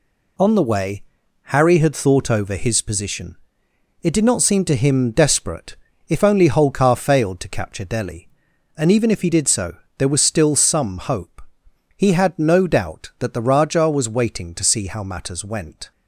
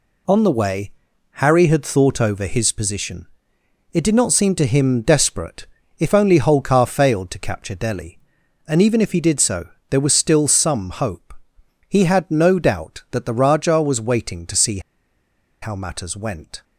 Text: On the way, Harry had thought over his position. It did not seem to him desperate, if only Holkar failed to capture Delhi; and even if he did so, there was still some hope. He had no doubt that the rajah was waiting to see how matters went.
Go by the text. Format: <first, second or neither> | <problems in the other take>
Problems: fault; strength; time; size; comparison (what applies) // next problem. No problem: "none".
first | pauses between "see" and "how"; noticeable; at 14.7 s; 0.83 s long